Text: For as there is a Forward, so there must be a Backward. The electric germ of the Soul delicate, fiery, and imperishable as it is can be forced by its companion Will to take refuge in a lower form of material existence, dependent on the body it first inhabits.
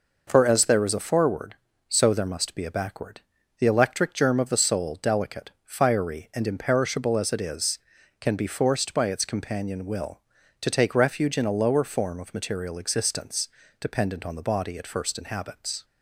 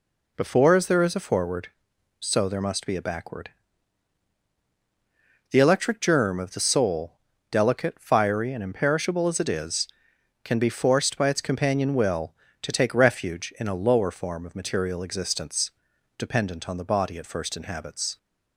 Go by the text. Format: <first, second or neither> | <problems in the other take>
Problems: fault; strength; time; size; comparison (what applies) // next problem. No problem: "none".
first | says "Before" for "For"; at 0.3 s // pauses between "Soul" and "delicate"; at 7.1 s; 0.38 s long